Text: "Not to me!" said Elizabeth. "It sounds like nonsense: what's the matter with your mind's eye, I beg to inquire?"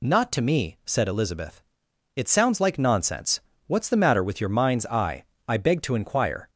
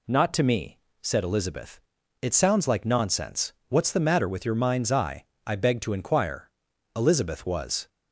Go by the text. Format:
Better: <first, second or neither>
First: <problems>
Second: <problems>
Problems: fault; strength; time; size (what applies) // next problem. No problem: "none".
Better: first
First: none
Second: goes on to say "Elizabeth was"; noticeable; from 6.9 s on; 0.94 s long